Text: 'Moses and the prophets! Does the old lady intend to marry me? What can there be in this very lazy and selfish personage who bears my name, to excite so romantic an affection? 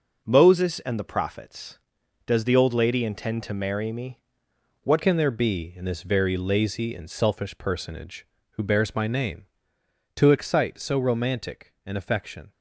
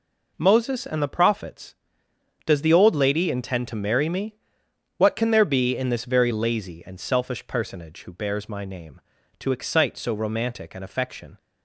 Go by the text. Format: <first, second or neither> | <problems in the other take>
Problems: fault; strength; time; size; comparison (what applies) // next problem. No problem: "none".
second | changes voice at "can"; from 5.0 s on; 7.5 s long